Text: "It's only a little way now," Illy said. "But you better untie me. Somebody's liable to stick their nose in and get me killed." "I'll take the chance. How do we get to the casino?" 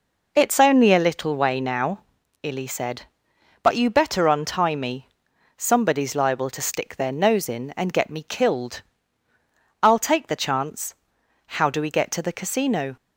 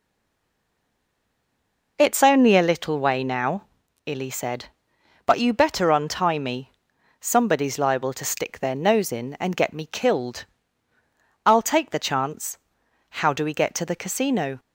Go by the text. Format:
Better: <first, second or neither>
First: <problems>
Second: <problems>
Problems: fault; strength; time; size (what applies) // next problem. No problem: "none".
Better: first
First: none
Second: stays silent before the first word; noticeable; until 1.9 s; 1.9 s long